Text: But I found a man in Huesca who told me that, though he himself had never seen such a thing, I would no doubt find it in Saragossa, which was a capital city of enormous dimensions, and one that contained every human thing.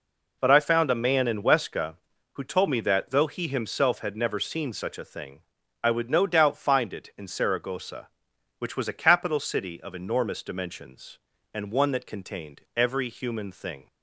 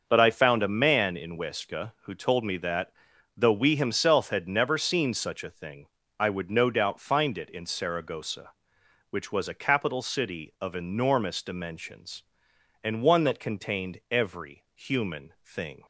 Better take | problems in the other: first | starts louder than the rest; until 1.0 s; 6.5 dB // says "we" for "he"; at 3.5 s

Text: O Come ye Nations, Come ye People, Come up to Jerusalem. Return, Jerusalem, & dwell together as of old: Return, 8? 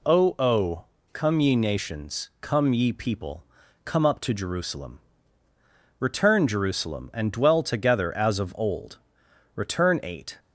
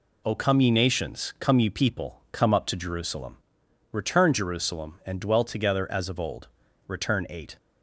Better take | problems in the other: second | says "O" twice; at 0.3 s

